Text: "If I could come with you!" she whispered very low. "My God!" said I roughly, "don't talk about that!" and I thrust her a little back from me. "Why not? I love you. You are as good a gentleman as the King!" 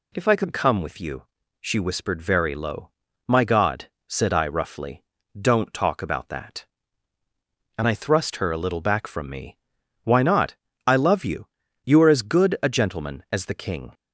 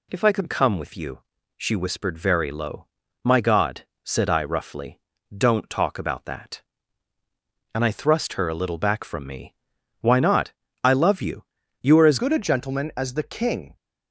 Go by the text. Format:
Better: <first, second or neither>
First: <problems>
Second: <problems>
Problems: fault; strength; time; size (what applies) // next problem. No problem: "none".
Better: first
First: none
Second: changes voice at "good"; from 12.1 s on; 1.6 s long